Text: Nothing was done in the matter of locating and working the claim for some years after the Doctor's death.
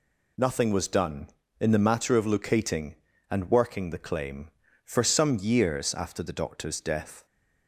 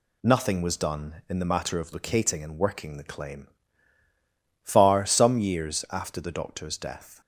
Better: first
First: none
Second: says "far" for "for"; at 4.6 s

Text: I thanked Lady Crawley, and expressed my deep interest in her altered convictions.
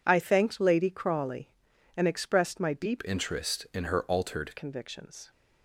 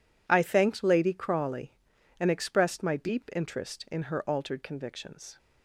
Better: second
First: changes voice from "interest" to "altered"; from 3.0 to 4.5 s; 1.5 s long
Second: none

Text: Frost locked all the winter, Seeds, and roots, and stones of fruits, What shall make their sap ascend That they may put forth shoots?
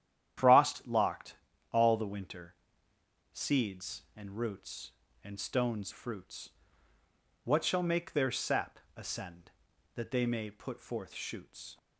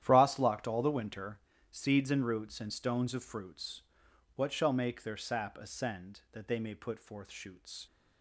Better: second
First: starts louder than the rest; strong; until 1.8 s; 10.5 dB // pauses between "locked" and "all"; at 1.3 s; 0.38 s long // skips "of"; at 5.9 s // pauses between "sap" and "ascend"; slight; at 8.7 s; 0.20 s long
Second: starts louder than the rest; strong; until 1.0 s; 11 dB

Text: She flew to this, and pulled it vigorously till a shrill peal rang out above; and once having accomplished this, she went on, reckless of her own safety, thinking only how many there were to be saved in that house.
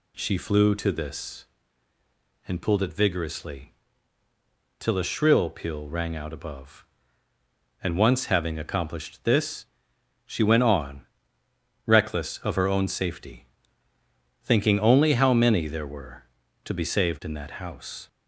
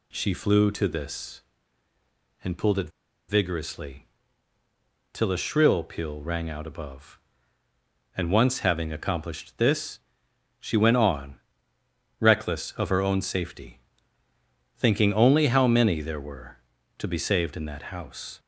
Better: first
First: pauses between "vigorously" and "till"; at 3.7 s; 1.0 s long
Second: pauses between "it" and "vigorously"; at 2.8 s; 0.38 s long // pauses between "vigorously" and "till"; at 4.0 s; 1.0 s long

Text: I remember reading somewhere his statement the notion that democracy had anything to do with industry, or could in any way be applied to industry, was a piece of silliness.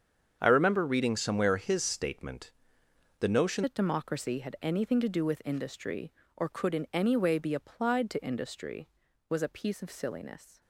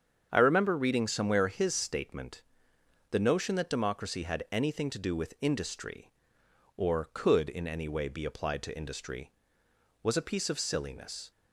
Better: second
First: starts louder than the rest; strong; until 1.4 s; 7.5 dB // pauses between "statement" and "the"; noticeable; at 2.5 s; 0.70 s long // changes voice at "that"; from 3.6 s on; 7.0 s long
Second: starts louder than the rest; strong; until 1.3 s; 7.5 dB // pauses between "statement" and "the"; noticeable; at 2.4 s; 0.70 s long

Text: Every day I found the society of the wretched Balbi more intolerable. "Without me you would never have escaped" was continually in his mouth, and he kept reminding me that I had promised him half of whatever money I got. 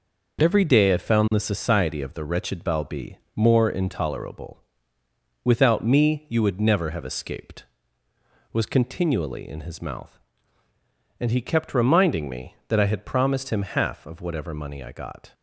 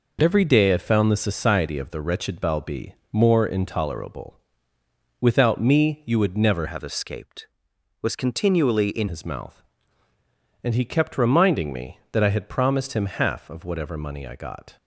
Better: first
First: pauses between "Balbi" and "more"; slight; at 3.1 s; 0.18 s long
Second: pauses between "Balbi" and "more"; slight; at 2.9 s; 0.18 s long // changes voice from "have" to "in"; from 6.6 to 9.0 s; 2.4 s long

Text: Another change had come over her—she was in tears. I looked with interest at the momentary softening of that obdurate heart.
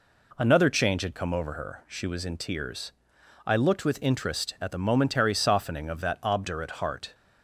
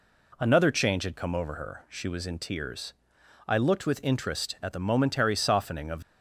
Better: first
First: none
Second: stops before "that obdurate heart"; at 6.0 s

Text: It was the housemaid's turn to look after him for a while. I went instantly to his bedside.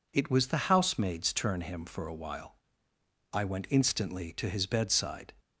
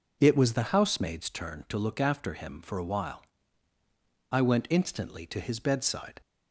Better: second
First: skips "to look after"; at 1.6 s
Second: none

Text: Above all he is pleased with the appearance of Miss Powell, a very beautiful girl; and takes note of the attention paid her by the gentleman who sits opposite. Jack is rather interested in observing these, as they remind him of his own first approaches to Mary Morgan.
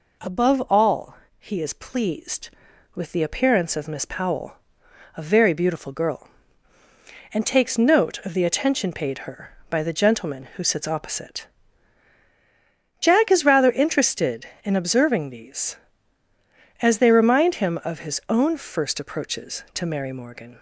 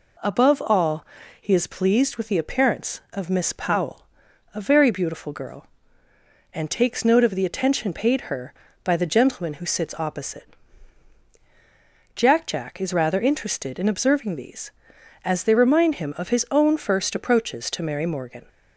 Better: first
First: pauses between "all" and "he"; slight; at 1.1 s; 0.22 s long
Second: pauses between "all" and "he"; slight; at 1.0 s; 0.36 s long // says "Jack" twice; at 12.4 s

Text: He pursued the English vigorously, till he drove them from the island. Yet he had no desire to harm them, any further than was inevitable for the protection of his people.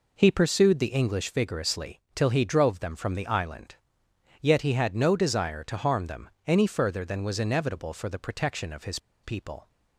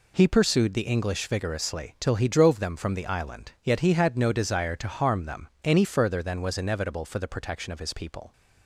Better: second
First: pauses between "his" and "people"; slight; at 8.9 s; 0.26 s long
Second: none

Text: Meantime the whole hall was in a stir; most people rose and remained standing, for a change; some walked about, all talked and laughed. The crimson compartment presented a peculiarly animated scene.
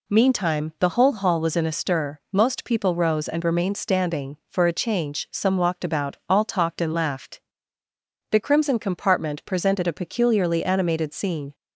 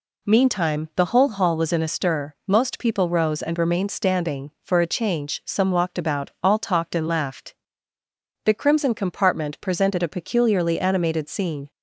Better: neither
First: none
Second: none

